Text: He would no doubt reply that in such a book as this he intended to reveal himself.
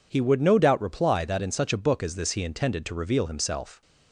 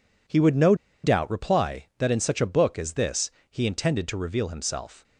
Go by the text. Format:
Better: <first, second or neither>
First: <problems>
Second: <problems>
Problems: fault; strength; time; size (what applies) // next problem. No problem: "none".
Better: first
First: none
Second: pauses between "no" and "doubt"; slight; at 0.7 s; 0.29 s long // pauses between "this" and "he"; slight; at 3.3 s; 0.18 s long